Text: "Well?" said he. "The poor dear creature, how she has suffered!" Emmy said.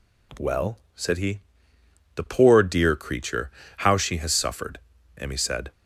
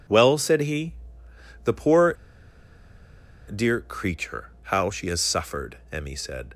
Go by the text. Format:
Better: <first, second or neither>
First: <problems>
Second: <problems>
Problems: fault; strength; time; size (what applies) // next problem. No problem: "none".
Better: first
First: none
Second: pauses between "poor" and "dear"; strong; at 2.1 s; 1.3 s long